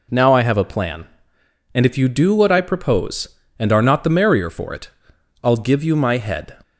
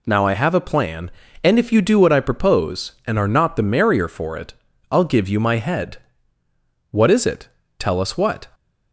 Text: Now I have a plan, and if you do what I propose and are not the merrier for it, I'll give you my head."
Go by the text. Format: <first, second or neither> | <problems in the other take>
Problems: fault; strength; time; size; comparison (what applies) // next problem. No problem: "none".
first | goes on to say "What is it Tell us what"; from 6.8 s on; 1.5 s long